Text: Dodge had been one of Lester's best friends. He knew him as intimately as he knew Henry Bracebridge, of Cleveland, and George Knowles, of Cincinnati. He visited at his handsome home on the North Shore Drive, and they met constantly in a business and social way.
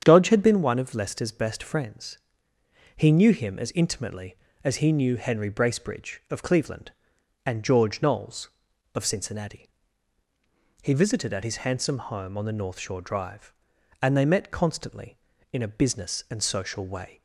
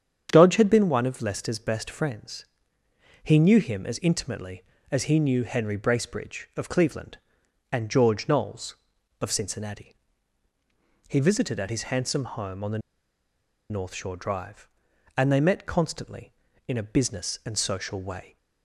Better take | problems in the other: first | starts louder than the rest; strong; until 1.3 s; 8.5 dB; strong in the first // pauses between "the" and "North"; noticeable; at 12.7 s; 0.91 s long

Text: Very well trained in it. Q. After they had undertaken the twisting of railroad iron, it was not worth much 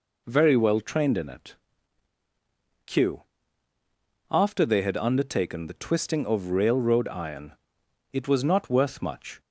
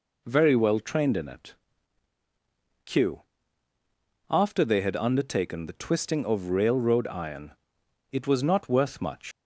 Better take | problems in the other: first | leaves "much" unfinished; at 9.3 s; 75 ms

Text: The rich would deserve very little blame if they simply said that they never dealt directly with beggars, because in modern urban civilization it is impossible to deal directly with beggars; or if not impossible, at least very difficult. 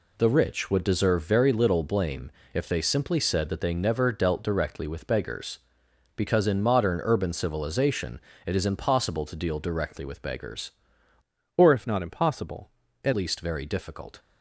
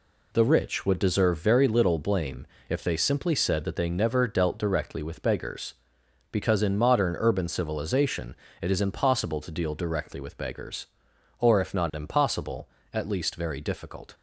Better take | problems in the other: second | pauses between "blame" and "if"; slight; at 2.2 s; 0.24 s long; slight in the second // pauses between "civilization" and "it"; slight; at 8.1 s; 0.26 s long; slight in the second // changes voice from "or" to "at"; from 11.5 to 13.1 s; 1.6 s long

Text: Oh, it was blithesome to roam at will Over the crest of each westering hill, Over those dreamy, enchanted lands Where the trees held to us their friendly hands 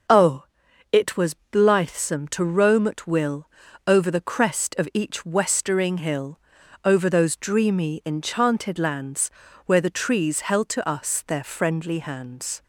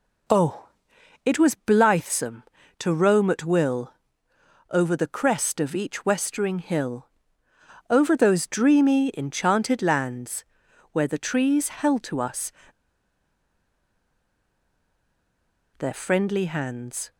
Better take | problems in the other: first | pauses between "will" and "Over"; noticeable; at 3.9 s; 0.78 s long; also in the first // pauses between "lands" and "Where"; noticeable; at 10.4 s; 0.48 s long; slight in the first // pauses between "us" and "their"; strong; at 12.5 s; 3.2 s long

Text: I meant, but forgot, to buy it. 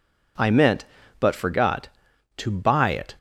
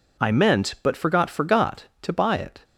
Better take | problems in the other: first | says "forgot" twice; at 1.2 s

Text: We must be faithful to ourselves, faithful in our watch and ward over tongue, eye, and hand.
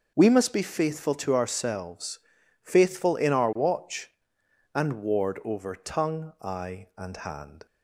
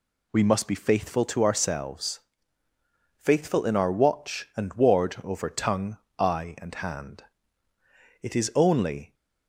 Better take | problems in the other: first | goes on to say "It is only"; noticeable; from 8.2 s on; 0.92 s long

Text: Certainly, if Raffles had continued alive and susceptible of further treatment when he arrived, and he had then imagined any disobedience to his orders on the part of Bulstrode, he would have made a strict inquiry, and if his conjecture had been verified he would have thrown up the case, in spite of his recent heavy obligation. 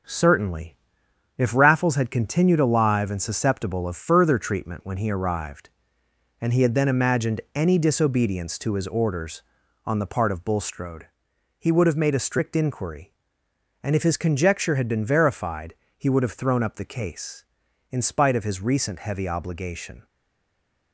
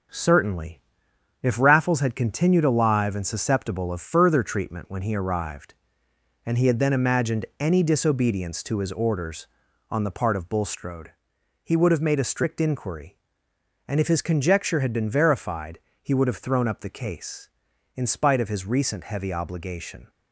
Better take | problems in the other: second | pauses between "verified" and "he"; slight; at 15.7 s; 0.24 s long; slight in the second // stays silent after the last word; slight; from 20.0 s on; 0.9 s long

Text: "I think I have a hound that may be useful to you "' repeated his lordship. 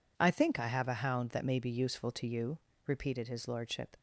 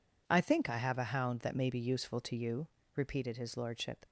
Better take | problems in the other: neither | none

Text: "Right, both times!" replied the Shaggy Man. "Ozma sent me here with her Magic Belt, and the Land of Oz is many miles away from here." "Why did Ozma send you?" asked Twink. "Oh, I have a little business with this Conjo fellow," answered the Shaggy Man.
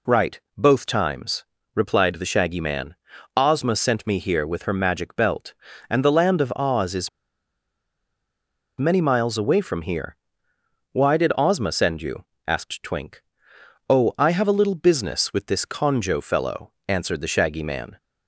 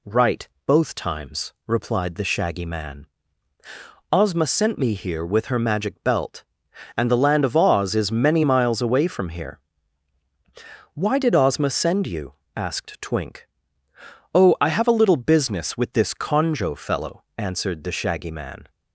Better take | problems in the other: second | pauses between "is" and "many"; strong; at 7.0 s; 1.6 s long

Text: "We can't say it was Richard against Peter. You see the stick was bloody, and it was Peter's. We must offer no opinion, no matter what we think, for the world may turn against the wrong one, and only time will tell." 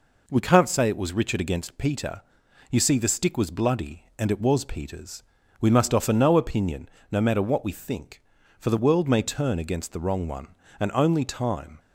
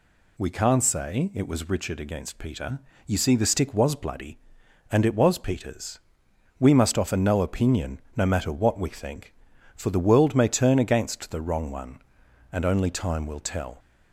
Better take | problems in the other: second | stops before "will tell"; at 11.7 s

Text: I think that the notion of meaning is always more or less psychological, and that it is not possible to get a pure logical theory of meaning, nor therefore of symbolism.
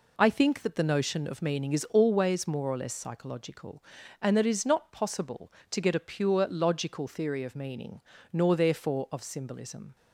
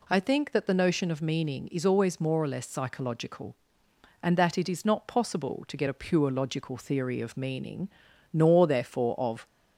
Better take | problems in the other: first | stops before "symbolism"; at 9.4 s

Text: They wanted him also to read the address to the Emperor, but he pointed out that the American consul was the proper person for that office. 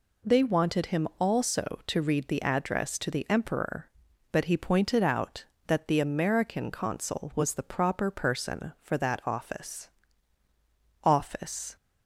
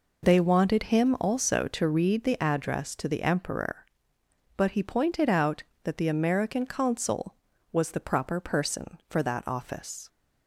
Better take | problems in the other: second | says "office" twice; at 11.0 s

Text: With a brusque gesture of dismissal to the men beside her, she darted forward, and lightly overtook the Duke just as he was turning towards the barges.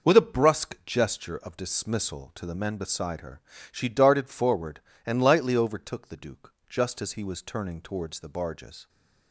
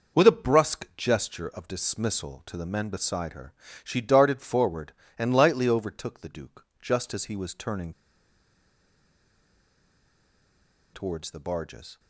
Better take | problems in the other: first | pauses between "Duke" and "just"; slight; at 6.6 s; 0.16 s long; slight in the first // pauses between "turning" and "towards"; strong; at 7.9 s; 3.0 s long

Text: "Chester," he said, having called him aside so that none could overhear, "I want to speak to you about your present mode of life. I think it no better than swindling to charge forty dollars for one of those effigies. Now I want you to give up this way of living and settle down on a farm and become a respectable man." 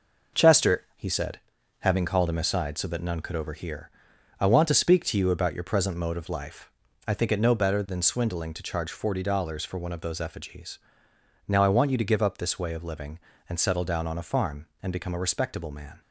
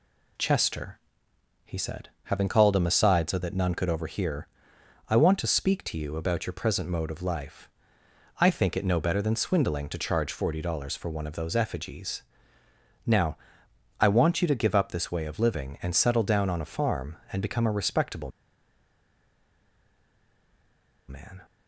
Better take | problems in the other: first | pauses between "Now" and "I"; noticeable; at 13.3 s; 0.60 s long // pauses between "respectable" and "man"; strong; at 18.3 s; 2.7 s long

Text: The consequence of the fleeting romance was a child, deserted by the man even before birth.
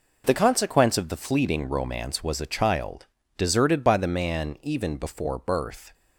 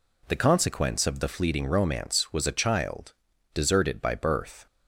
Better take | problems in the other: first | skips "the man even before"; at 4.1 s

